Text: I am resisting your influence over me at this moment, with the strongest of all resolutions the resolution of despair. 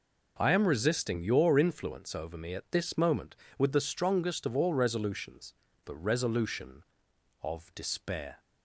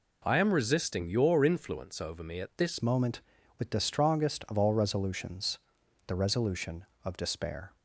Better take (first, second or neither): first